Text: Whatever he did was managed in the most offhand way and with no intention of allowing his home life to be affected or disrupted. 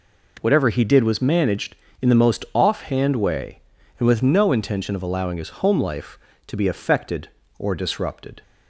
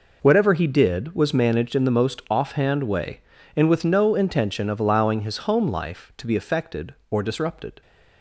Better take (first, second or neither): neither